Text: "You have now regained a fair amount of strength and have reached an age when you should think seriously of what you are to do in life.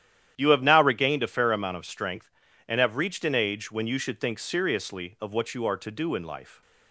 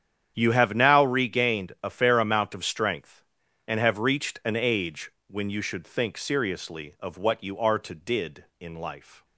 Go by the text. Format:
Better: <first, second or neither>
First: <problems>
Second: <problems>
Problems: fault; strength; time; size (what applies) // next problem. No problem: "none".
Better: first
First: starts louder than the rest; strong; until 1.3 s; 10.5 dB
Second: starts louder than the rest; strong; until 1.3 s; 9.5 dB // pauses between "age" and "when"; slight; at 5.1 s; 0.16 s long // says "did" for "do"; at 7.9 s